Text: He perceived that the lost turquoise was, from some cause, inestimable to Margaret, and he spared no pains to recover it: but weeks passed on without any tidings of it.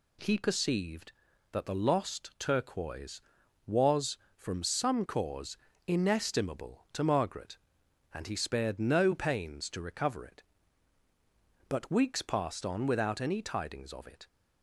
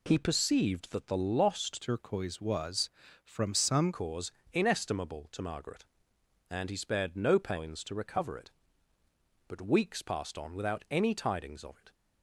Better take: first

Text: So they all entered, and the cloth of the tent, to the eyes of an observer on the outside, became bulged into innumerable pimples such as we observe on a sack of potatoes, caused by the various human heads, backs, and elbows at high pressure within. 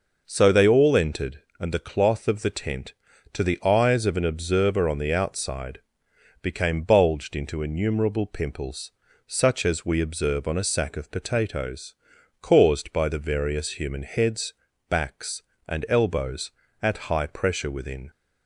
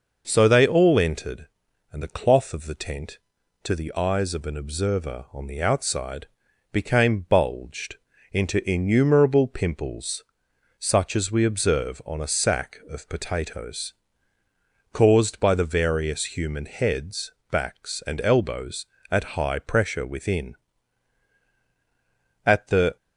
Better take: first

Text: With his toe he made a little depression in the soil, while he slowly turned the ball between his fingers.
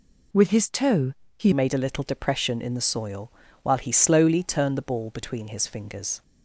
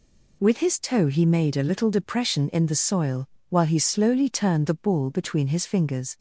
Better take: second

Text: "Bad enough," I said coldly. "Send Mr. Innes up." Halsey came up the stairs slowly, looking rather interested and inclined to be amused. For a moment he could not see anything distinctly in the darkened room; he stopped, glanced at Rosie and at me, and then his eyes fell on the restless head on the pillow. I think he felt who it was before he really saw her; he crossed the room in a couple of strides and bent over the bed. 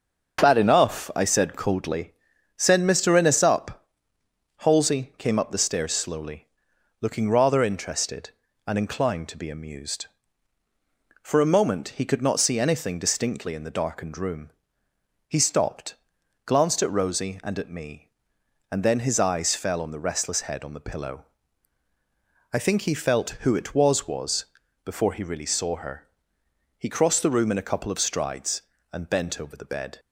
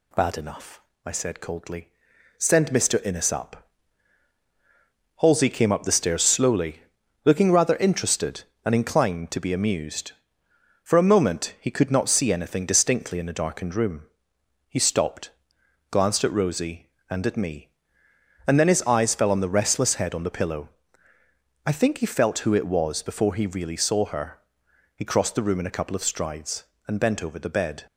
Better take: second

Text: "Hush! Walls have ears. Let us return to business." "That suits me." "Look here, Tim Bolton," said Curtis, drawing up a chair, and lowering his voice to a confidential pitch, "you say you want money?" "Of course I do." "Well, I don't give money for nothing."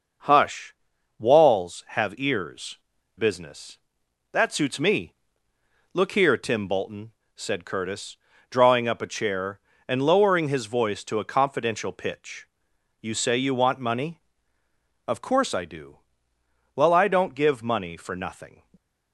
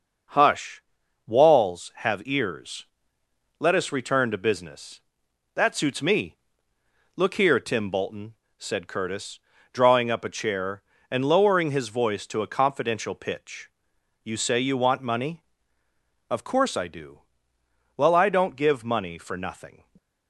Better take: second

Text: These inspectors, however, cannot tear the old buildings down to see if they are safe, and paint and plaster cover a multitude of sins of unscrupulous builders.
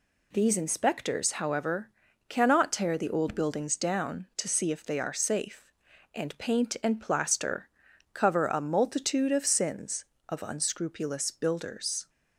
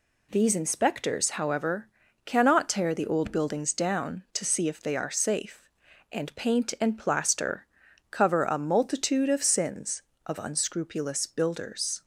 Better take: neither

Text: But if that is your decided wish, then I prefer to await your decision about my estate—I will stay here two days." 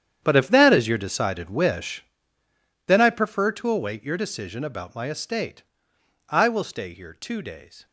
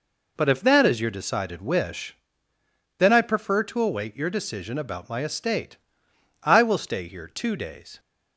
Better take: second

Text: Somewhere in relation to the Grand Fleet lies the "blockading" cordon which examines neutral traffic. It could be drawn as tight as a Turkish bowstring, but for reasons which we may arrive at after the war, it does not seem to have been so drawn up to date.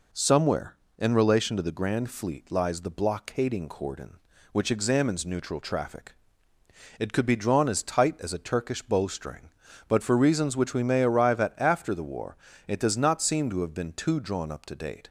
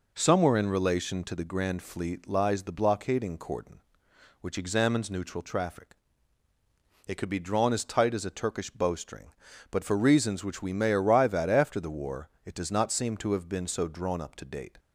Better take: second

